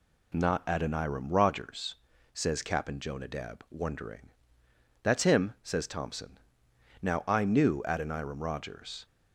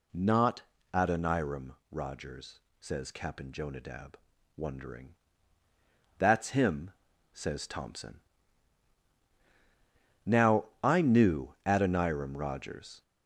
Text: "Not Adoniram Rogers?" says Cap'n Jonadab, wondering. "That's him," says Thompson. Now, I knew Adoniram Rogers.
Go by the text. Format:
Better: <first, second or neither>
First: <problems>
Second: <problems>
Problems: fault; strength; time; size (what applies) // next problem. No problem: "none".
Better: first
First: none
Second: gets louder; noticeable; throughout; 5 dB // pauses between "Not" and "Adoniram"; slight; at 0.6 s; 0.28 s long // pauses between "Adoniram" and "Rogers"; slight; at 1.7 s; 0.16 s long